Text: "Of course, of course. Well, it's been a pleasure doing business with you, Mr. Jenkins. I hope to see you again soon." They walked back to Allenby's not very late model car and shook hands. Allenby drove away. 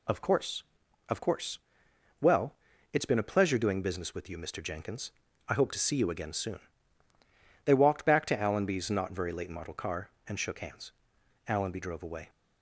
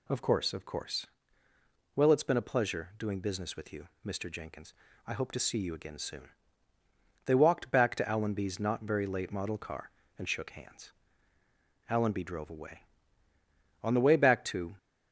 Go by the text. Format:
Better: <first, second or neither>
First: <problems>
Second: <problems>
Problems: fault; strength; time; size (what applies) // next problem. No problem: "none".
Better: first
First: none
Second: goes on to say "On the way back to"; noticeable; from 13.8 s on; 0.94 s long